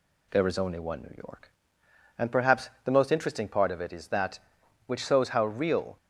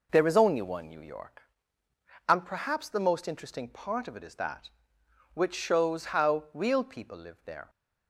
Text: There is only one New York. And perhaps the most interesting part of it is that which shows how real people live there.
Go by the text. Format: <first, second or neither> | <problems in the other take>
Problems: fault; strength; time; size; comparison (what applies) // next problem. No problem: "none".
second | pauses between "perhaps" and "the"; slight; at 2.6 s; 0.16 s long // stops before "people live there"; at 5.9 s